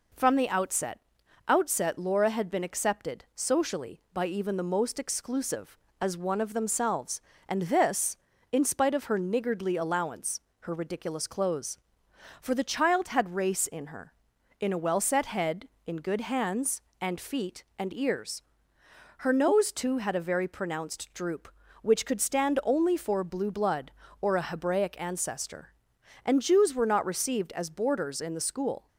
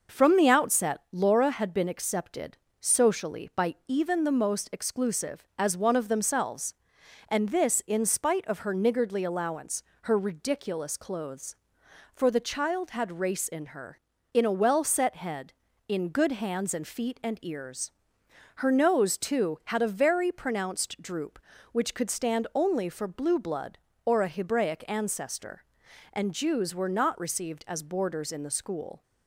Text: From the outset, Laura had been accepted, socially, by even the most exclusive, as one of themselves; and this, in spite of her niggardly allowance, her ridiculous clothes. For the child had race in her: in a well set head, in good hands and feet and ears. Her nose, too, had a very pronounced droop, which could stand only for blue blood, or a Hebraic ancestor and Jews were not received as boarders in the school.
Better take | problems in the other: second | says "outset" twice; at 1.4 s

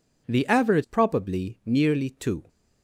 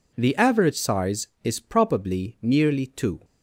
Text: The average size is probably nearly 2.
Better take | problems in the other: second | skips "size is"; at 0.8 s

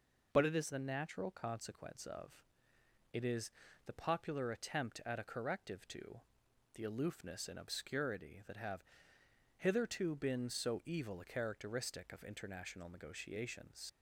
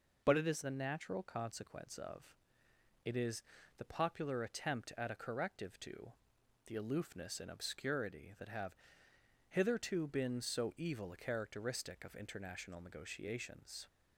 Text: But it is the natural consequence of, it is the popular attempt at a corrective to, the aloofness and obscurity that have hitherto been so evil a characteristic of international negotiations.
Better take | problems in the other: second | pauses between "is" and "the"; slight; at 3.5 s; 0.36 s long; slight in the second // pauses between "have" and "hitherto"; noticeable; at 8.8 s; 0.74 s long; noticeable in the second // leaves "negotiations" unfinished; at 13.8 s; 55 ms

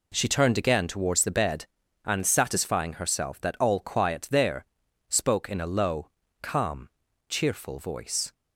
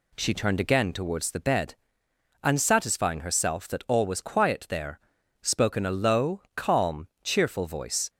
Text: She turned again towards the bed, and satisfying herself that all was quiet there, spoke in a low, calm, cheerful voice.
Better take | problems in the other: second | skips "was"; at 3.7 s

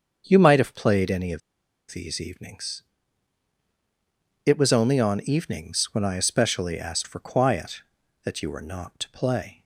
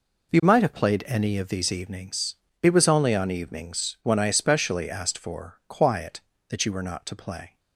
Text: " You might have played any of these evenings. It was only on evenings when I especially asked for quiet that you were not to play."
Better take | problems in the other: second | starts louder than the rest; until 1.2 s; 7 dB // pauses between "of" and "these"; noticeable; at 1.4 s; 0.51 s long

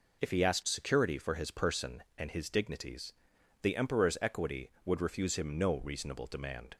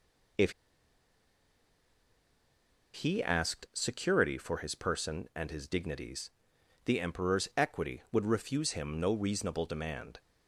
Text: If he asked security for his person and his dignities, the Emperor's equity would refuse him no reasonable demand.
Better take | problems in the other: first | pauses between "If" and "he"; strong; at 0.5 s; 2.4 s long

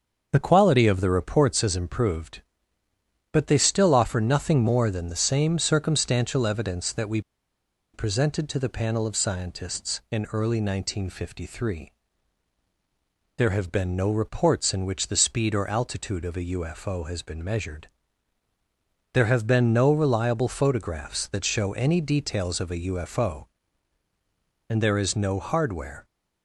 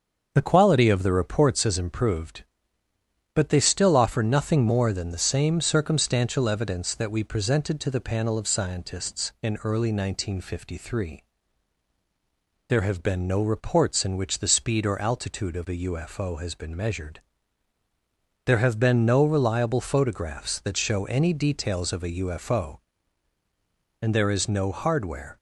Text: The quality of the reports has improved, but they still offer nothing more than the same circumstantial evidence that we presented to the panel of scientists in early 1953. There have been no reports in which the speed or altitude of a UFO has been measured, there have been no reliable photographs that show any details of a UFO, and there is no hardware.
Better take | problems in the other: second | starts louder than the rest; until 1.3 s; 6.5 dB; also in the second // pauses between "we" and "presented"; noticeable; at 7.1 s; 0.73 s long

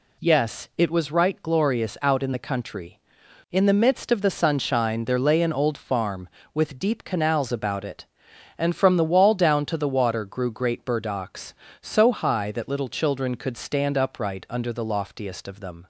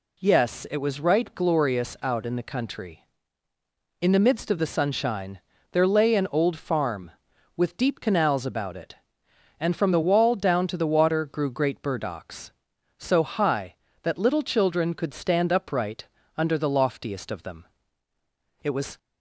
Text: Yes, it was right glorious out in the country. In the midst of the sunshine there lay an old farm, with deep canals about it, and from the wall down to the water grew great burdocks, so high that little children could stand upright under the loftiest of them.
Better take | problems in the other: first | pauses between "sunshine" and "there"; slight; at 5.3 s; 0.32 s long // pauses between "upright" and "under"; slight; at 16.0 s; 0.32 s long // goes on to say "It was"; slight; from 18.6 s on; 0.34 s long

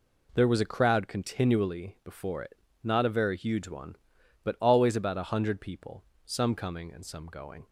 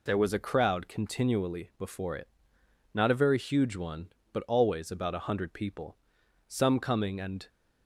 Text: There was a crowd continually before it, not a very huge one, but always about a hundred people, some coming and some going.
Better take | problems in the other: first | stops before "some going"; at 7.4 s

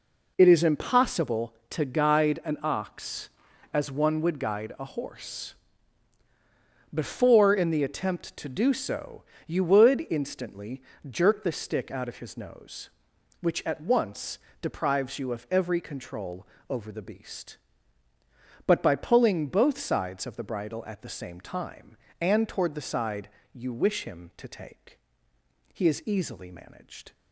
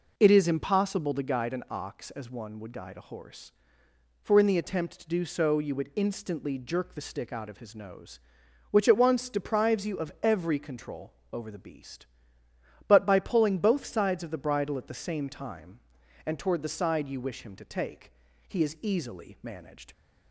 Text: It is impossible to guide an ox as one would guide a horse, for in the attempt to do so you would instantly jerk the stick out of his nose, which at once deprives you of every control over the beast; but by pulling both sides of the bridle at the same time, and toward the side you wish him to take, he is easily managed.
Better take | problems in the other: second | says "before" for "for"; at 6.9 s // pauses between "so" and "you"; slight; at 9.2 s; 0.24 s long // pauses between "instantly" and "jerk"; slight; at 10.8 s; 0.28 s long // pauses between "once" and "deprives"; slight; at 14.3 s; 0.22 s long // pauses between "control" and "over"; slight; at 16.4 s; 0.24 s long; slight in the second // pauses between "side" and "you"; slight; at 23.2 s; 0.24 s long

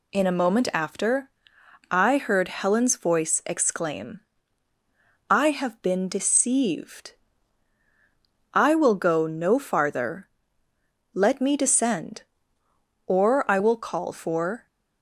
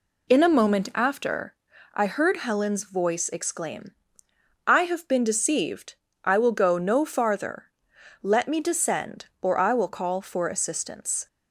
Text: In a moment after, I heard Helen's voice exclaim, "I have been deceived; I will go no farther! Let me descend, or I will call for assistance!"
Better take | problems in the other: second | stops before "assistance"; at 14.6 s

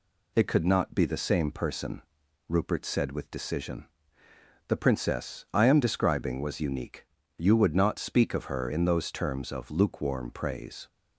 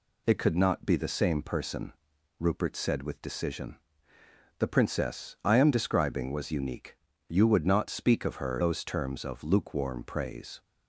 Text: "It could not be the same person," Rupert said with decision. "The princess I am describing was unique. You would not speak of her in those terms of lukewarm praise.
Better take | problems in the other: first | skips "in"; at 8.5 s

